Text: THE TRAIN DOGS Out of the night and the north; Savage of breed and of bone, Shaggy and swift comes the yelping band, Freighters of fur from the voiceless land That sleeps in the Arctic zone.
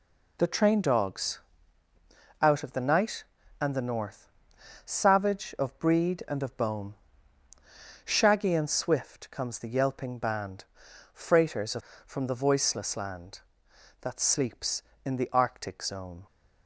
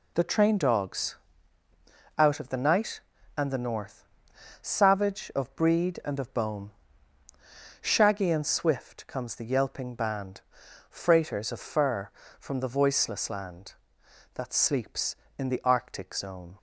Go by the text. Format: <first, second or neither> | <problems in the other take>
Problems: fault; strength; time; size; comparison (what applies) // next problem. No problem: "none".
second | pauses between "DOGS" and "Out"; at 1.4 s; 1.0 s long; also in the second // skips "fur"; at 11.9 s